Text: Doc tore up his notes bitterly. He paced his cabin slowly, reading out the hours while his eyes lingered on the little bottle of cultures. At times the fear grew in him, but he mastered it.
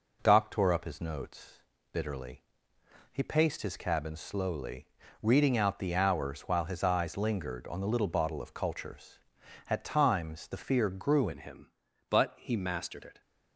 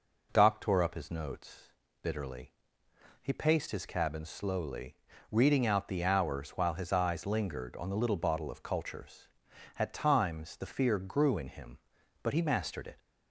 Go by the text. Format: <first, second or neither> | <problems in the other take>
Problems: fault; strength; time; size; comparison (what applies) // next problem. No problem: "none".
second | pauses between "notes" and "bitterly"; slight; at 1.5 s; 0.34 s long; slight in the second // changes voice at "in"; from 11.3 s on; 1.9 s long